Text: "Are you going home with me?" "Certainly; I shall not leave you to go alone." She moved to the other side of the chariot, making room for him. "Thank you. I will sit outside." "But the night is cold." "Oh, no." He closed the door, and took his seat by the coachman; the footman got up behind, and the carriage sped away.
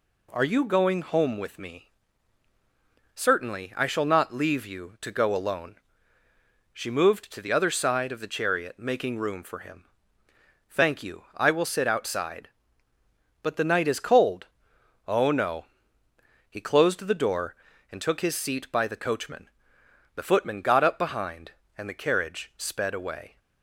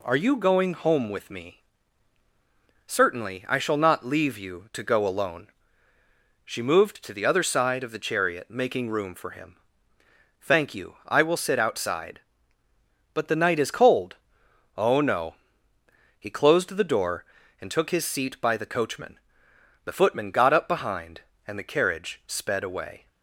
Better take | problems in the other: neither | none

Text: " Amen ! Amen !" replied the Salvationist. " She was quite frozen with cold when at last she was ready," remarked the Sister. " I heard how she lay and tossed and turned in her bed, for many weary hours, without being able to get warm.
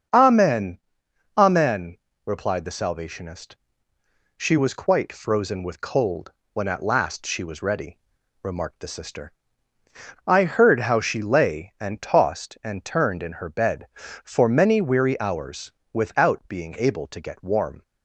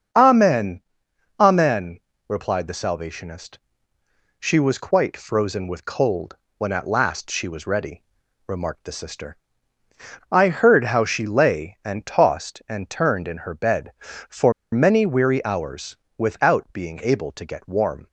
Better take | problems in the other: first | starts louder than the rest; strong; until 1.7 s; 10 dB; strong in the first // pauses between "cold" and "when"; slight; at 6.3 s; 0.22 s long; slight in the first // pauses between "for" and "many"; slight; at 14.5 s; 0.20 s long

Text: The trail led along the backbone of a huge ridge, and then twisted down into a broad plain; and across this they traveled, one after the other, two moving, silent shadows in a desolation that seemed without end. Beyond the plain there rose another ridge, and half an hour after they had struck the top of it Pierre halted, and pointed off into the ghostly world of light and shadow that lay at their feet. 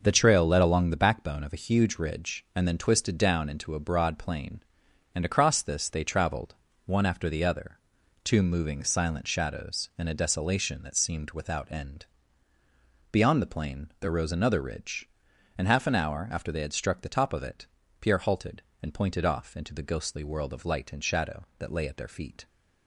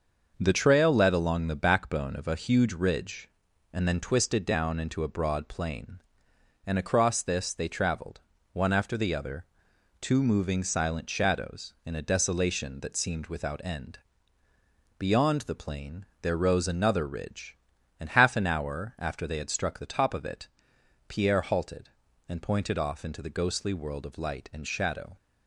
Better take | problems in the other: first | starts louder than the rest; until 1.4 s; 6 dB // pauses between "plain" and "there"; slight; at 16.0 s; 0.16 s long // pauses between "it" and "Pierre"; noticeable; at 20.4 s; 0.58 s long; slight in the first // stops before "that lay at their feet"; at 25.1 s

